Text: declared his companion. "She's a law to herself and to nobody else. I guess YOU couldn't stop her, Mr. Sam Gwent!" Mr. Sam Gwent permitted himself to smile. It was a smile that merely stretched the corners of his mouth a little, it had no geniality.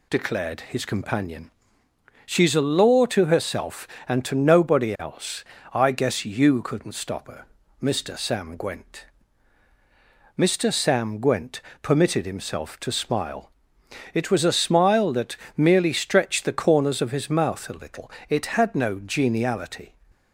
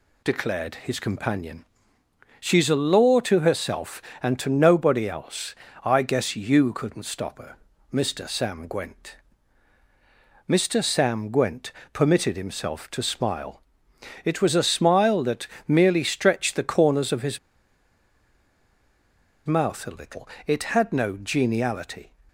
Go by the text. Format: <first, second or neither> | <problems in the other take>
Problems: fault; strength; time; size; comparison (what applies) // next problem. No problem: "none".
first | pauses between "Gwent" and "permitted"; slight; at 11.7 s; 0.20 s long; slight in the first // pauses between "that" and "merely"; slight; at 15.4 s; 0.20 s long; slight in the first // pauses between "his" and "mouth"; strong; at 17.3 s; 2.0 s long